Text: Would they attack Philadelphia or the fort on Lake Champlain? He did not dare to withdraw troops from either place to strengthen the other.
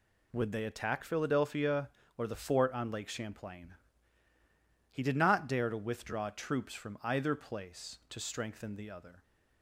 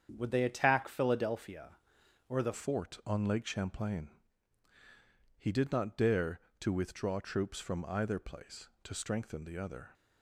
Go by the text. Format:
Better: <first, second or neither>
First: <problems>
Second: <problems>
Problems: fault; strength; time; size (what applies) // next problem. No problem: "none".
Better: first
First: none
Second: starts louder than the rest; strong; until 1.1 s; 8 dB // changes voice at "fort"; from 2.5 s on; 7.4 s long